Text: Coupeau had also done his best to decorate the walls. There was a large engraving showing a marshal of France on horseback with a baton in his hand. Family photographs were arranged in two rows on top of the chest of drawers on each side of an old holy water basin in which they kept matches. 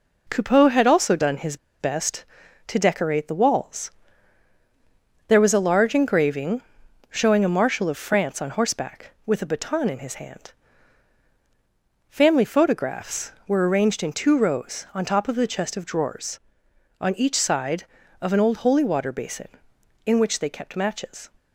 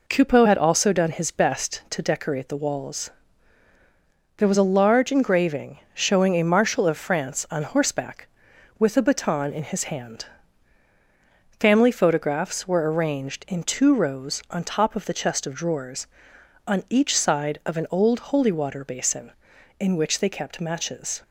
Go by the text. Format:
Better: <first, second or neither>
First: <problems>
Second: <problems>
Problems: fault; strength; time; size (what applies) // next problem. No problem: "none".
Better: second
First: pauses between "his" and "best"; slight; at 1.5 s; 0.24 s long // pauses between "engraving" and "showing"; noticeable; at 6.6 s; 0.48 s long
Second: none